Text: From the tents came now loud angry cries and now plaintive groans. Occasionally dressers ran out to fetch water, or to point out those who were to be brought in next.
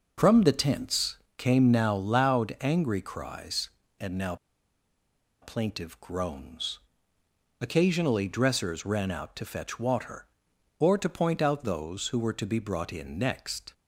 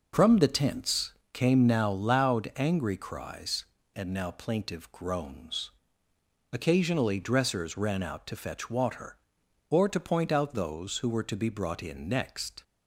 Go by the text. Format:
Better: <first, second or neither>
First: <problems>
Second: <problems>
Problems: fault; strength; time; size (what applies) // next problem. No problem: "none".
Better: second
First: pauses between "tents" and "came"; slight; at 1.1 s; 0.22 s long // pauses between "now" and "plaintive"; at 4.3 s; 1.0 s long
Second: pauses between "tents" and "came"; slight; at 1.1 s; 0.22 s long